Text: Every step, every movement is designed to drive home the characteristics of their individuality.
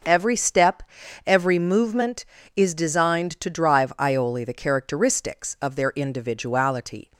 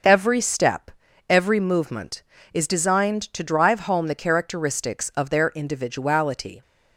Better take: second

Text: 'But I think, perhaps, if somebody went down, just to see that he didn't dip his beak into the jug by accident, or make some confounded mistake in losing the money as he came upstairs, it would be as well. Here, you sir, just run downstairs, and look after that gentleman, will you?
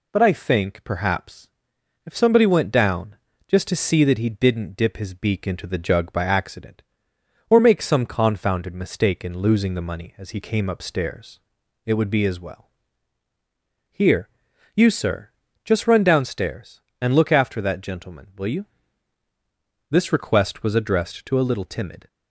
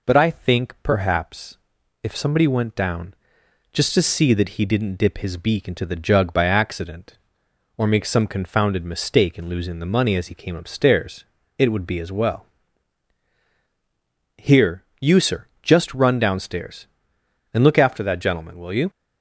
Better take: second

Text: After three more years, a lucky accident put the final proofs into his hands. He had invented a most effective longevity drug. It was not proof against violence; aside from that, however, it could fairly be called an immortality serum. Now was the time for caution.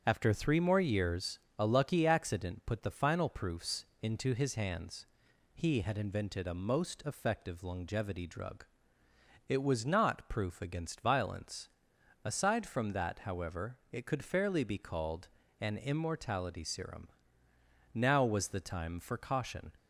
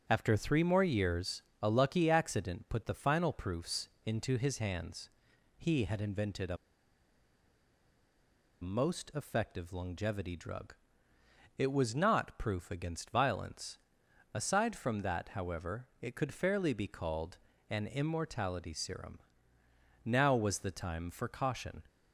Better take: first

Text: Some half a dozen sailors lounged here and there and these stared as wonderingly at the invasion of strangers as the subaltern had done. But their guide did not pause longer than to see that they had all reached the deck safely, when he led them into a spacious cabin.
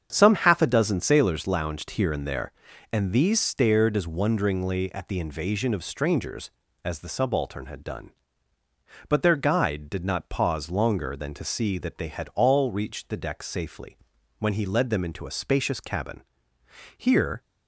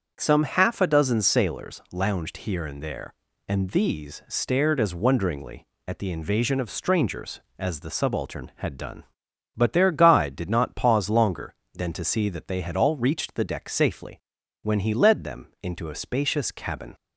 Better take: second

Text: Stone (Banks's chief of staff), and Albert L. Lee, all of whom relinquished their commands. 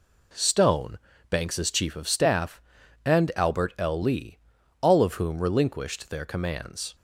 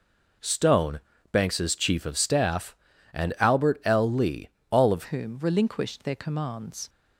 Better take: first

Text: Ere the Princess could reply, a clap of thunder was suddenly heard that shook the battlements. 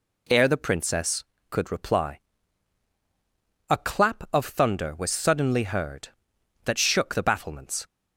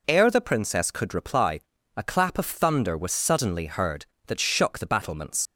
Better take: first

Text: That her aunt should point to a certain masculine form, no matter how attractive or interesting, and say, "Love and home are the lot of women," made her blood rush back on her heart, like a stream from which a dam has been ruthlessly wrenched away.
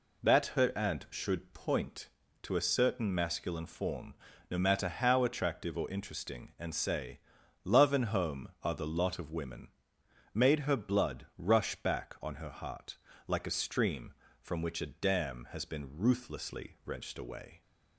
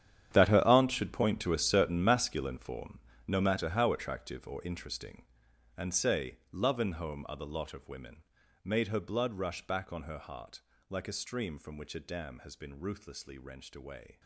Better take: first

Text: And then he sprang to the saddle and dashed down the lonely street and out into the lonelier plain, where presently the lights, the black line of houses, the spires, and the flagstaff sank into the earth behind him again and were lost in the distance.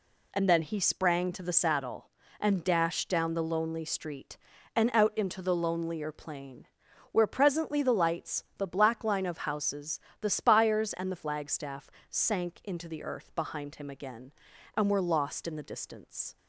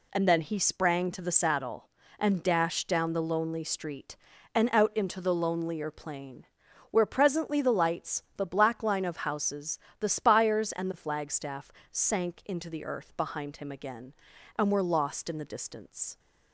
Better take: neither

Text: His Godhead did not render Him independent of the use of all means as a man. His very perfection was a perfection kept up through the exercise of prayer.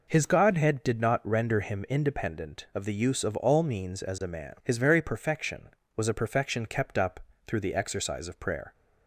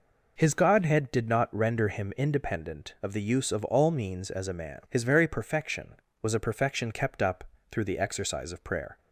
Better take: neither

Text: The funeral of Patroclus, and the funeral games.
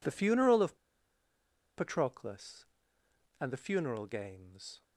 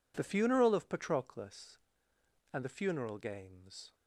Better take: second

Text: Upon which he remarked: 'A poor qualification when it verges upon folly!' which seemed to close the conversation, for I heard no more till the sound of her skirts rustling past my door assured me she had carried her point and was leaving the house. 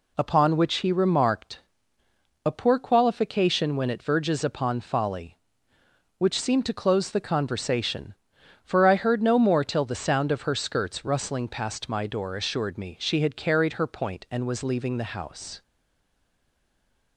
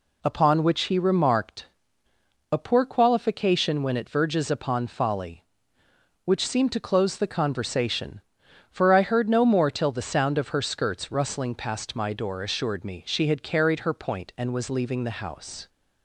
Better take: second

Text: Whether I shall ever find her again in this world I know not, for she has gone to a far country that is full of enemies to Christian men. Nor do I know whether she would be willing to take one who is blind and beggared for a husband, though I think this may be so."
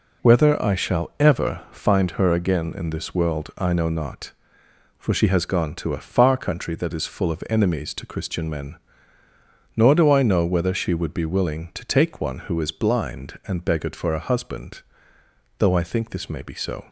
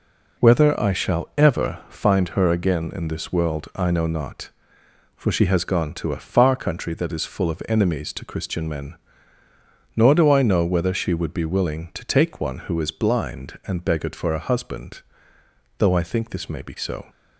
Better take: neither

